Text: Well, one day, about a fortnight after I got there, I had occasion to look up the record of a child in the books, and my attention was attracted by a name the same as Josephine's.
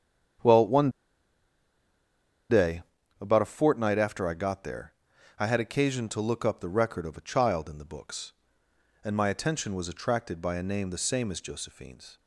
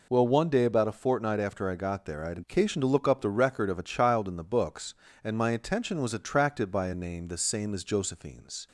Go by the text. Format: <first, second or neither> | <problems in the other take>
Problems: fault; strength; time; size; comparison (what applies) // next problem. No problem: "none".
second | starts louder than the rest; strong; until 3.3 s; 8.5 dB // pauses between "one" and "day"; strong; at 0.8 s; 1.6 s long